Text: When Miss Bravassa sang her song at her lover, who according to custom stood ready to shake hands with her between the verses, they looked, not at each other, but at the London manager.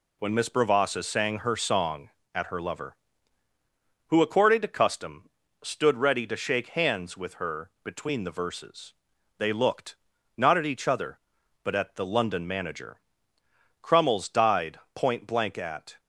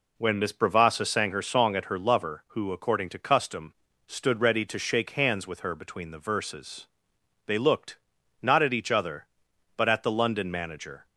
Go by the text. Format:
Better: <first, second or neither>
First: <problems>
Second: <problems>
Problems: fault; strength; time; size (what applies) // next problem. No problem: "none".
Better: second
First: pauses between "custom" and "stood"; slight; at 5.2 s; 0.34 s long // pauses between "her" and "between"; slight; at 7.6 s; 0.16 s long // goes on to say "Crummles died point blank at"; strong; from 13.7 s on; 2.2 s long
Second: pauses between "custom" and "stood"; slight; at 3.7 s; 0.32 s long